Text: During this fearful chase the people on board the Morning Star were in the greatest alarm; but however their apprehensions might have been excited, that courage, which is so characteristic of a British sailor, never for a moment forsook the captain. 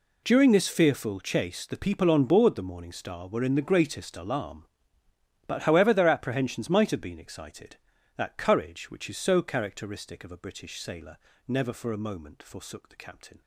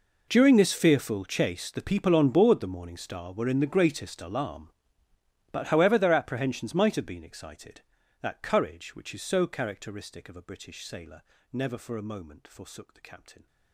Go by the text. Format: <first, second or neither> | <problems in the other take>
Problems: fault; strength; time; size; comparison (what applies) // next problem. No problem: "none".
first | gets quieter; strong; throughout; 20.5 dB